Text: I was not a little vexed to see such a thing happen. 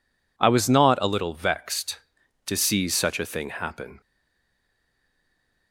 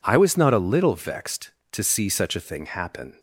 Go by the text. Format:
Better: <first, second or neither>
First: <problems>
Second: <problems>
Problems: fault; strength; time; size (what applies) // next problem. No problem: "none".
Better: second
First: stays silent after the last word; noticeable; from 4.0 s on; 1.7 s long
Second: none